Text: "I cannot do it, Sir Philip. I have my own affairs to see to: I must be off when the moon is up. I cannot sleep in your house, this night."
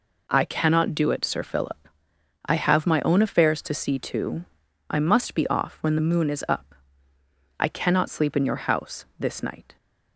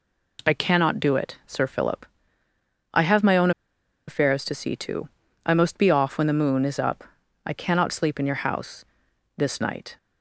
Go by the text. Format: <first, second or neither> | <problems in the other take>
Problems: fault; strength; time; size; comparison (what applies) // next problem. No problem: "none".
first | pauses between "own" and "affairs"; noticeable; at 3.5 s; 0.57 s long